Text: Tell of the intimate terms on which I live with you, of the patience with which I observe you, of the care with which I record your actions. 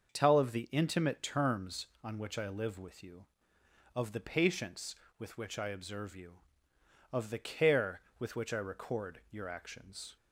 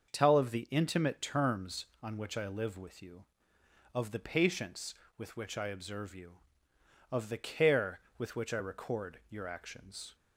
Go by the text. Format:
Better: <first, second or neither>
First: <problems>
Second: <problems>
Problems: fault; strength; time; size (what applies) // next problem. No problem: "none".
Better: neither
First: starts louder than the rest; until 1.1 s; 6.5 dB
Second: starts louder than the rest; until 1.1 s; 6.5 dB